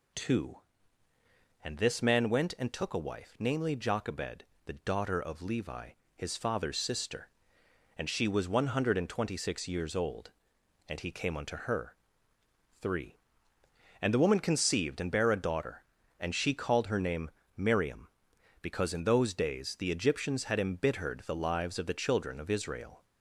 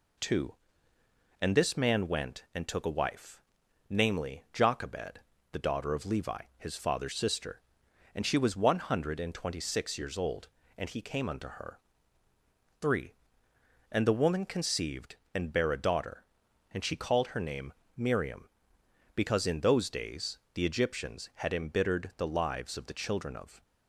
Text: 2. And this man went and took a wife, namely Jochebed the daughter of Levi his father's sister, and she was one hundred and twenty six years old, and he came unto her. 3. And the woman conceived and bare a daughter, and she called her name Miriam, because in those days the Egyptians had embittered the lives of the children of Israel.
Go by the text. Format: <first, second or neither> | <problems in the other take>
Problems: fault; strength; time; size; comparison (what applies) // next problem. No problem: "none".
first | pauses between "Jochebed" and "the"; slight; at 5.1 s; 0.32 s long; slight in the first // pauses between "Levi" and "his"; slight; at 6.3 s; 0.18 s long; slight in the first // pauses between "name" and "Miriam"; slight; at 17.7 s; 0.24 s long; slight in the first // pauses between "days" and "the"; slight; at 20.3 s; 0.16 s long // stops before "Israel"; at 23.6 s